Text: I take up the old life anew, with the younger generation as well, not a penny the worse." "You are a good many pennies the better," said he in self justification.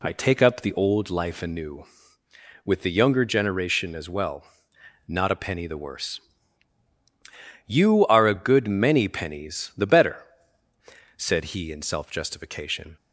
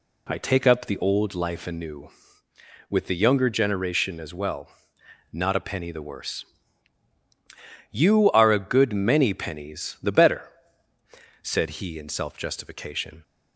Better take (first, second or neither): neither